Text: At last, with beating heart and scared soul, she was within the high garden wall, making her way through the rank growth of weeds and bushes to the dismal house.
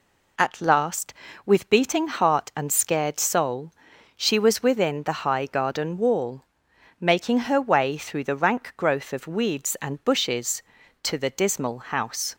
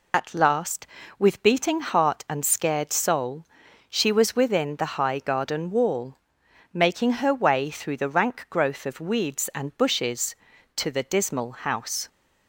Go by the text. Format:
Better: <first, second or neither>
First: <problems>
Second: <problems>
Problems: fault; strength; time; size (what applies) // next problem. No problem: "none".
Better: first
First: none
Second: loses the start of "At"; at 0.1 s; 35 ms